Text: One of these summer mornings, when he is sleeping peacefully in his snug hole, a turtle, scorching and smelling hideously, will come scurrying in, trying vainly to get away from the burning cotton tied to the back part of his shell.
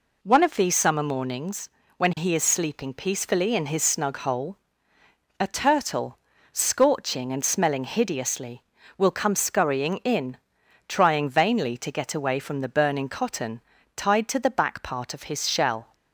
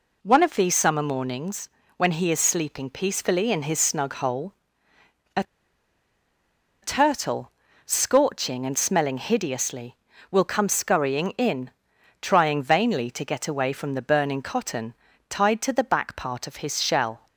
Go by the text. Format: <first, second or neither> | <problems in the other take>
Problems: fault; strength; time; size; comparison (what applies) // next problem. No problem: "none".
first | pauses between "a" and "turtle"; strong; at 5.4 s; 1.3 s long // pauses between "cotton" and "tied"; slight; at 14.9 s; 0.36 s long; slight in the first